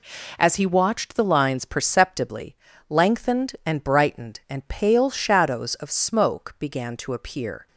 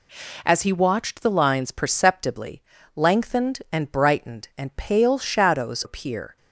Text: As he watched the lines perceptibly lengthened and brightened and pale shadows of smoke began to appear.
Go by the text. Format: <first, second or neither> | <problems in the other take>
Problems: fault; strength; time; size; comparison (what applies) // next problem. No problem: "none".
first | pauses between "perceptibly" and "lengthened"; slight; at 2.6 s; 0.34 s long; slight in the first // skips "of smoke began to"; at 5.8 s